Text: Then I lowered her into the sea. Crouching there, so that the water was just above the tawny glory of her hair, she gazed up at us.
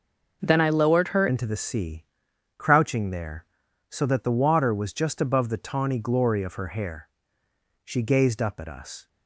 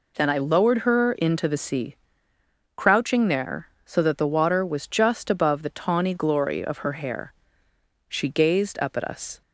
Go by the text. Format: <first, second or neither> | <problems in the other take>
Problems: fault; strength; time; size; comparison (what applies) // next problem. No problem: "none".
second | changes voice at "into"; from 1.2 s on; 7.8 s long